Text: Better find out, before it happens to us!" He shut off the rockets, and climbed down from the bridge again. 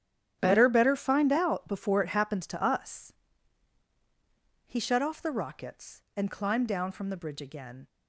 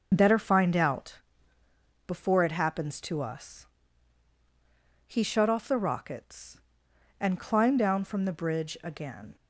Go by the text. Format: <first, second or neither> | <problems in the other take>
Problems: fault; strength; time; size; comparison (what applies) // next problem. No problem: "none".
second | starts louder than the rest; strong; until 1.4 s; 9.5 dB; noticeable in the second // says "Better" twice; at 0.6 s